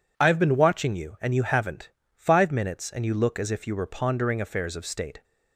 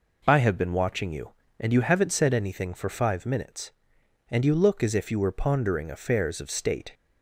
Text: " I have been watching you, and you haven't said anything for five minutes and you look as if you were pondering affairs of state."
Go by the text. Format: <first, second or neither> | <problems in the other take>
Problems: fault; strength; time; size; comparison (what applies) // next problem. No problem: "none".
second | skips "said anything for"; at 2.0 s